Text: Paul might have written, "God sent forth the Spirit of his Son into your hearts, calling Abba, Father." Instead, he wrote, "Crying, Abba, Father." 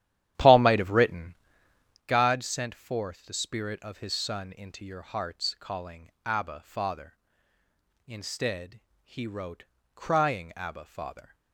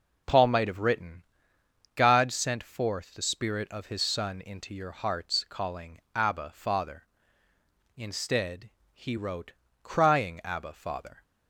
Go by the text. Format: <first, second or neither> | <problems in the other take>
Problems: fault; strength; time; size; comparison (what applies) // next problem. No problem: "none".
second | starts louder than the rest; strong; until 2.0 s; 11.5 dB // pauses between "calling" and "Abba"; slight; at 6.0 s; 0.16 s long; slight in the second